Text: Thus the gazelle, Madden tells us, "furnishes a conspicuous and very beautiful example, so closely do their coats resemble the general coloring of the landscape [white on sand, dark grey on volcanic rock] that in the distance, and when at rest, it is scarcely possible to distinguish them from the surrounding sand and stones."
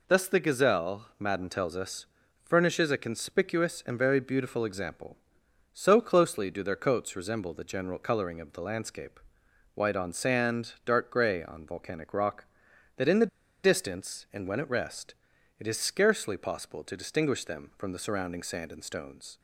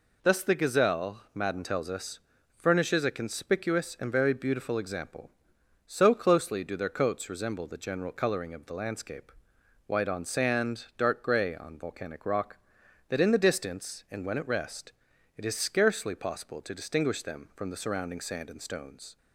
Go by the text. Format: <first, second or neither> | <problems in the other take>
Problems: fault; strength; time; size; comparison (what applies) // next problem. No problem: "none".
second | pauses between "landscape" and "white"; noticeable; at 9.1 s; 0.54 s long; noticeable in the second // pauses between "the" and "distance"; at 13.2 s; 0.37 s long